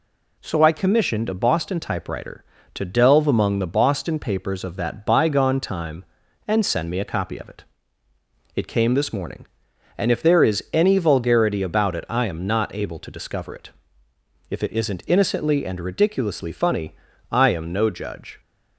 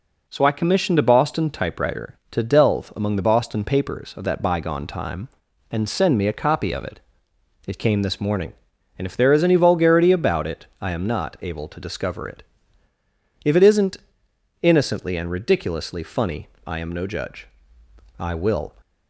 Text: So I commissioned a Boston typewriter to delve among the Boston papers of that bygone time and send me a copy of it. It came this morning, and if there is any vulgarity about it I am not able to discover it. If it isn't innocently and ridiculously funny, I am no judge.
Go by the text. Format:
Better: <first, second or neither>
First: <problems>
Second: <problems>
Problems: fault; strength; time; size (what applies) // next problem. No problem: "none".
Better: first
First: none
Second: pauses between "it" and "I"; slight; at 10.6 s; 0.16 s long // pauses between "isn't" and "innocently"; noticeable; at 13.9 s; 0.64 s long // goes on to say "I will"; from 18.1 s on; 0.56 s long